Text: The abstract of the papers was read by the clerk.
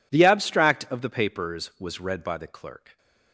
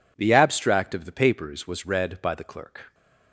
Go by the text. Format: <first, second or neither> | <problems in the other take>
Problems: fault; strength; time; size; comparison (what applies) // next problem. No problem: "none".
neither | none